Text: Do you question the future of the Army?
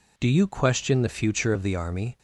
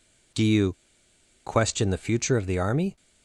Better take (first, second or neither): first